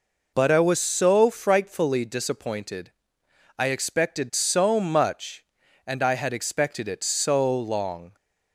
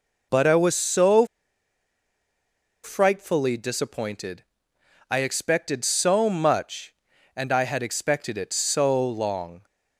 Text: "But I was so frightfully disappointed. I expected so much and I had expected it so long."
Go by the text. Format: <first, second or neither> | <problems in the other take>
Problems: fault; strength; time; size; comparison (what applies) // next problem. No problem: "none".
first | pauses between "so" and "frightfully"; strong; at 1.2 s; 1.5 s long